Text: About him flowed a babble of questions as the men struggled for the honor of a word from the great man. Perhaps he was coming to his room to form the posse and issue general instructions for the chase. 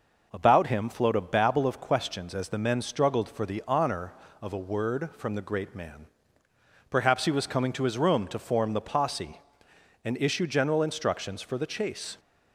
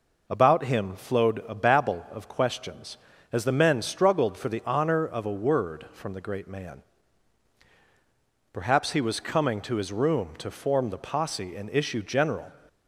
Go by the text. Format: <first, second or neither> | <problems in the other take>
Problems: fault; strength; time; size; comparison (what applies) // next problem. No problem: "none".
first | stops before "instructions for the chase"; at 12.6 s